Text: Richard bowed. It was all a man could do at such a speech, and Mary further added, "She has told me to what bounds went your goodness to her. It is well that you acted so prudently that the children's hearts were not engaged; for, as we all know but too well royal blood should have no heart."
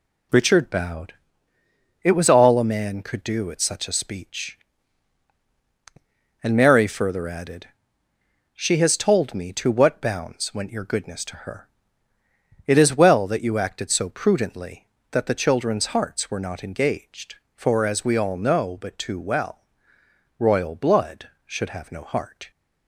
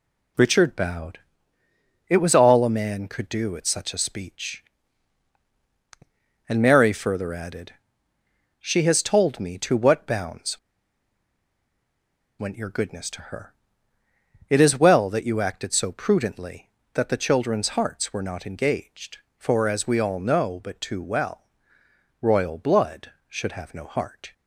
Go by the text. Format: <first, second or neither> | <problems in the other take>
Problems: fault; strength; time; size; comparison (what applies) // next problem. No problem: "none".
first | pauses between "bounds" and "went"; strong; at 10.5 s; 1.8 s long // pauses between "well" and "royal"; noticeable; at 21.4 s; 0.76 s long; noticeable in the first